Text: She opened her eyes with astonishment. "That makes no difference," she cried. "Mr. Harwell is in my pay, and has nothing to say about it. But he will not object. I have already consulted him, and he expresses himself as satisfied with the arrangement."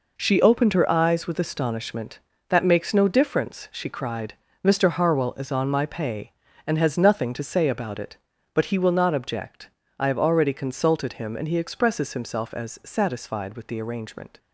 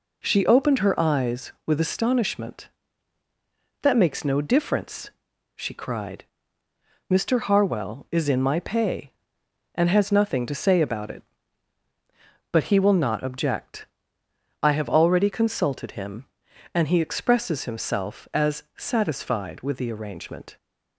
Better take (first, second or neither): second